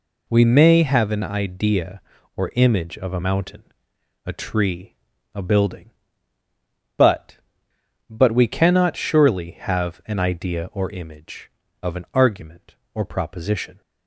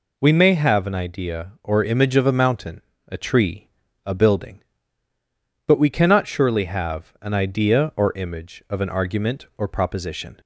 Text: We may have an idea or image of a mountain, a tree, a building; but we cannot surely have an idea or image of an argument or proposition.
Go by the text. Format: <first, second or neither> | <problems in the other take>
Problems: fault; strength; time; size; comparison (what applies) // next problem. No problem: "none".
second | says "but" twice; at 8.0 s